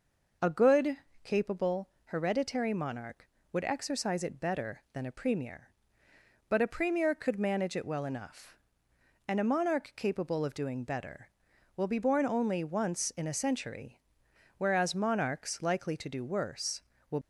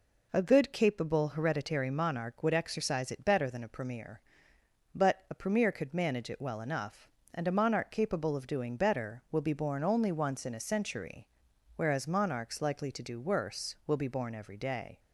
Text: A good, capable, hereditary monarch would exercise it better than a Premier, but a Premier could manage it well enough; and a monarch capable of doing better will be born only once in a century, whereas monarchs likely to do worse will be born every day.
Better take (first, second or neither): second